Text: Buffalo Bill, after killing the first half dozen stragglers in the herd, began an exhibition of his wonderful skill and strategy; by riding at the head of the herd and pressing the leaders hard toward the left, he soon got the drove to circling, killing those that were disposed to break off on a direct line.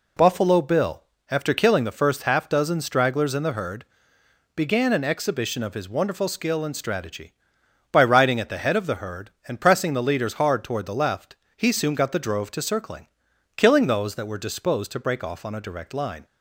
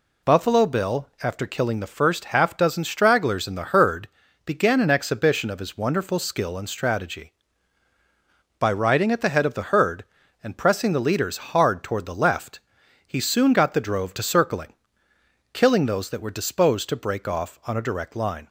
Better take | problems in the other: neither | none

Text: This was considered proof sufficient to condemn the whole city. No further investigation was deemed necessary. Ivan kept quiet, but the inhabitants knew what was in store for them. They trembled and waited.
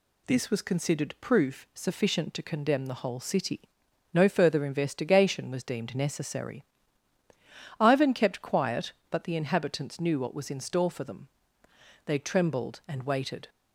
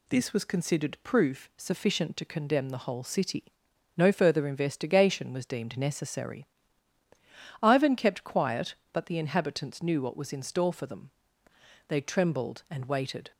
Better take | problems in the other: neither | none

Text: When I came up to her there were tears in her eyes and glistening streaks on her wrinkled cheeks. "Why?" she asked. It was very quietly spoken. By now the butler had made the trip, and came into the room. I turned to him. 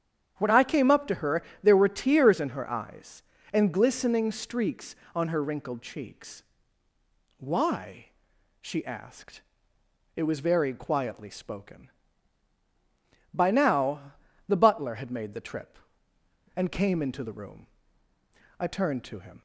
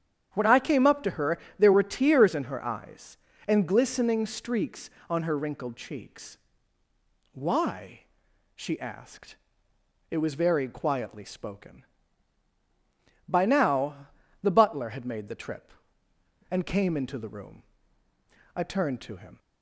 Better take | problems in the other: neither | starts louder than the rest; strong; the same in both // pauses between "her" and "there"; slight; the same in both // pauses between "now" and "the"; slight; the same in both

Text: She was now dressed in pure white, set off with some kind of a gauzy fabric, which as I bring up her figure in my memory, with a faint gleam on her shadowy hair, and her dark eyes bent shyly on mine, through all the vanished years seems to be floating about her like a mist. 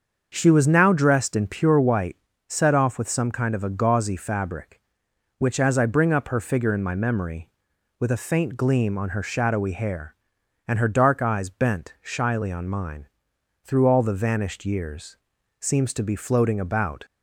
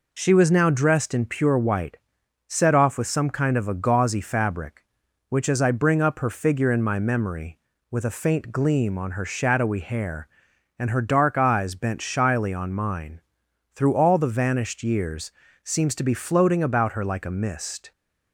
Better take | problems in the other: second | starts louder than the rest; until 1.3 s; 6.5 dB // pauses between "years" and "seems"; at 15.1 s; 0.42 s long; slight in the second // stops before "her like a mist"; at 17.0 s

